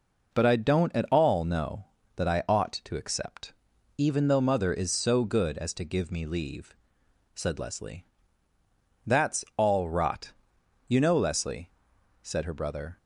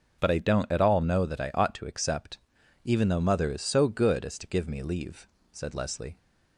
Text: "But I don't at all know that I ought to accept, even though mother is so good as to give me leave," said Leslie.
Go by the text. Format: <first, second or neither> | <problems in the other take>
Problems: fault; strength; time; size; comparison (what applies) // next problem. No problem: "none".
second | goes on to say "That's all rot you know Leslie said her brother"; strong; from 9.0 s on; 3.9 s long